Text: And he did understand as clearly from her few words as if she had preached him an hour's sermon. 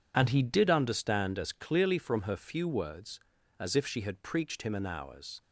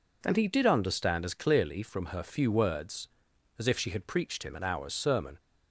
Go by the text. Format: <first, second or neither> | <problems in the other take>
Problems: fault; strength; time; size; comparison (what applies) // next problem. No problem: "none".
second | stops before "sermon"; at 5.4 s